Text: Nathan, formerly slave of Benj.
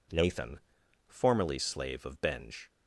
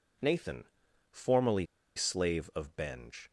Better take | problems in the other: first | pauses between "formerly" and "slave"; slight; at 1.6 s; 0.31 s long

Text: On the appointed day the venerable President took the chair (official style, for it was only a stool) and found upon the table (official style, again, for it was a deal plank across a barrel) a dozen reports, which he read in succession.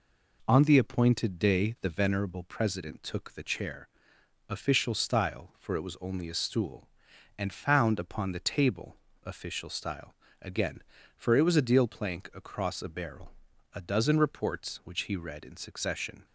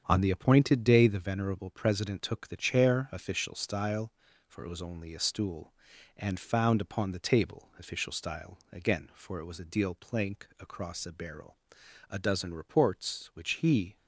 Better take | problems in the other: first | starts louder than the rest; strong; until 1.0 s; 8 dB // stops before "read in succession"; at 13.9 s

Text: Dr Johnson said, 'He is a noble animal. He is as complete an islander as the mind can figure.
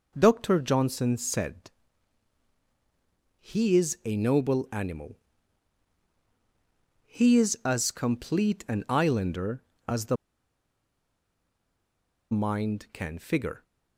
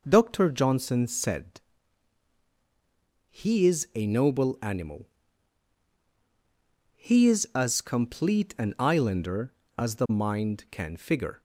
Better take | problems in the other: second | pauses between "the" and "mind"; strong; at 10.1 s; 2.1 s long

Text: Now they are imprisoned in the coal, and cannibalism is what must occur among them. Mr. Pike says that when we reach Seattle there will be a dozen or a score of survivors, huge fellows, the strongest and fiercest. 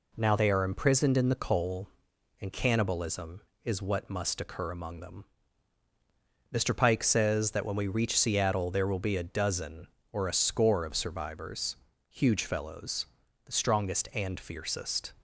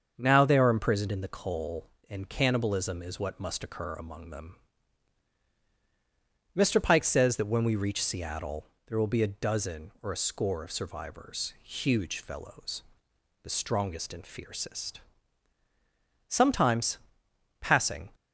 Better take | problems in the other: first | starts louder than the rest; until 1.1 s; 6.5 dB // pauses between "Seattle" and "there"; slight; at 8.6 s; 0.20 s long // goes on to say "Sometimes passing"; strong; from 16.2 s on; 1.8 s long

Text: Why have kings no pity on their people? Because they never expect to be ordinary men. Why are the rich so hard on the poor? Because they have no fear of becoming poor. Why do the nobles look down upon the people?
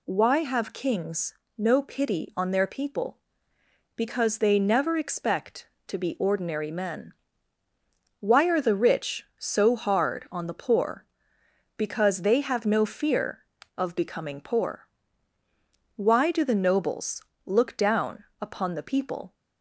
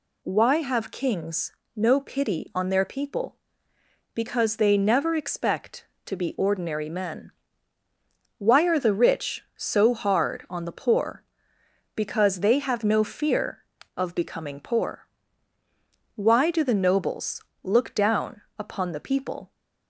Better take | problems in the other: neither | pauses between "kings" and "no"; slight; the same in both // pauses between "nobles" and "look"; slight; the same in both // pauses between "down" and "upon"; slight; the same in both

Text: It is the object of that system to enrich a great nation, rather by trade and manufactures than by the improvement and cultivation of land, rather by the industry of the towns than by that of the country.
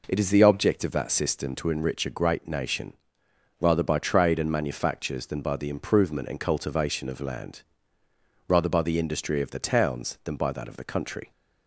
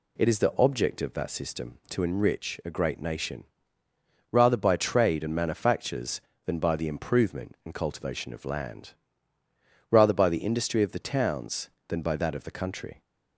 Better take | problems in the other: neither | none

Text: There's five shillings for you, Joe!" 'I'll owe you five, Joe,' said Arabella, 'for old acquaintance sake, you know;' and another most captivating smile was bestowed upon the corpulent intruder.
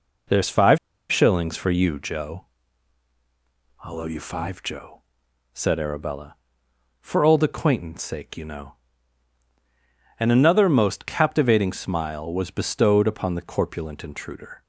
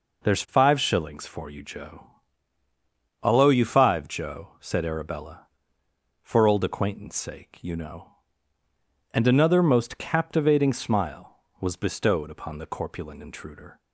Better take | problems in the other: second | pauses between "five" and "shillings"; slight; at 0.7 s; 0.31 s long

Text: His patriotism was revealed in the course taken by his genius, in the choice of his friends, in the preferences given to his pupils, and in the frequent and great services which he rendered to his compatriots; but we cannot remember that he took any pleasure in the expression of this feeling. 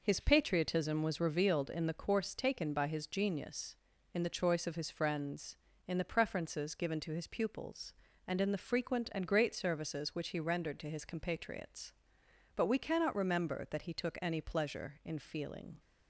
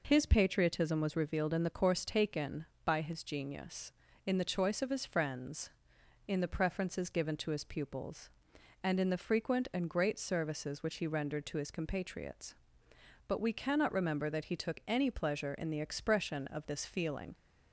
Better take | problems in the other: second | skips "the expression of this"; at 15.1 s

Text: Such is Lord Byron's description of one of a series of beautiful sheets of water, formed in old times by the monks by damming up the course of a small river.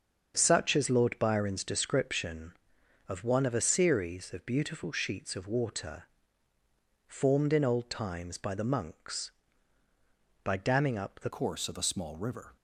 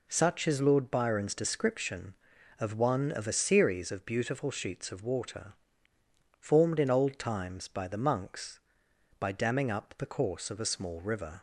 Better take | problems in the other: second | starts louder than the rest; until 1.3 s; 7 dB // changes voice at "course"; from 11.2 s on; 1.3 s long

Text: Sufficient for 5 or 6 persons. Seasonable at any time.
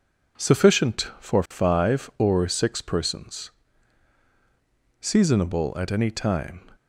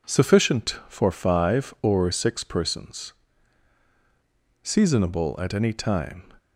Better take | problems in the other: neither | none

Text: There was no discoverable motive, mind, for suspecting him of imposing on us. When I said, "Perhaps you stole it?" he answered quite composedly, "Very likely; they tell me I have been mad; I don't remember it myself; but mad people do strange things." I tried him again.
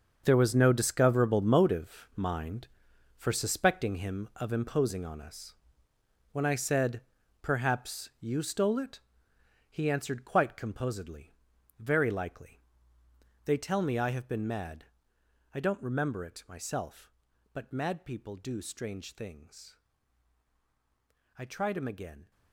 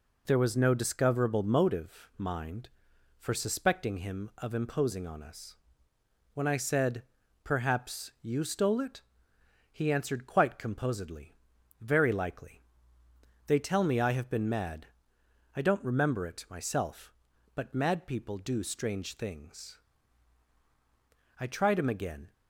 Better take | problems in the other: second | gets quieter; strong; throughout; 13 dB

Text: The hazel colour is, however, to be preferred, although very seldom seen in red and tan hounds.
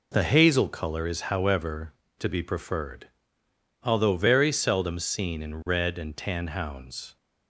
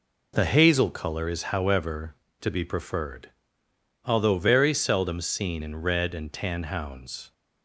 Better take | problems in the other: neither | none

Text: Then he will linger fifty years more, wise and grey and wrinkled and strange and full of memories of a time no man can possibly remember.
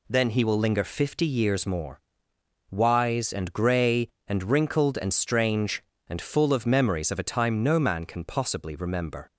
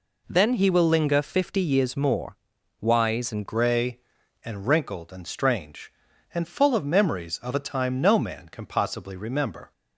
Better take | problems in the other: first | changes voice at "grey"; from 3.4 s on; 6.3 s long

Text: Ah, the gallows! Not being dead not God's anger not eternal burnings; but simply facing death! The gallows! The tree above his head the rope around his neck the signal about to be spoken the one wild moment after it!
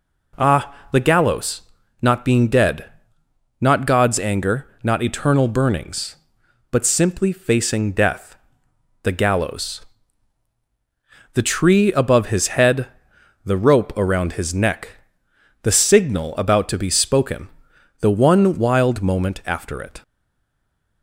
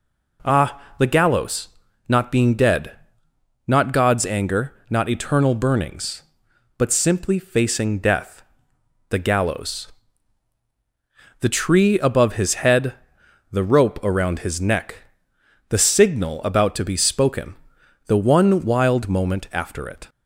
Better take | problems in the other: second | pauses between "dead" and "not"; noticeable; at 2.9 s; 0.70 s long; noticeable in the second // pauses between "anger" and "not"; slight; at 4.6 s; 0.16 s long; slight in the second // pauses between "head" and "the"; noticeable; at 12.8 s; 0.56 s long; noticeable in the second // pauses between "neck" and "the"; noticeable; at 14.8 s; 0.74 s long; noticeable in the second // pauses between "spoken" and "the"; noticeable; at 17.4 s; 0.52 s long; noticeable in the second // stays silent after the last word; from 20.0 s on; 1.0 s long

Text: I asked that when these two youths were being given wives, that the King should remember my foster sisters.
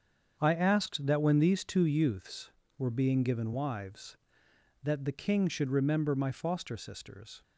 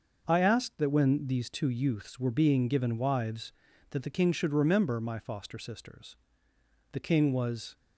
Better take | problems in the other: first | starts louder than the rest; noticeable; until 1.2 s; 6 dB; strong in the first // goes on to say "The King was"; noticeable; from 6.9 s on; 0.82 s long

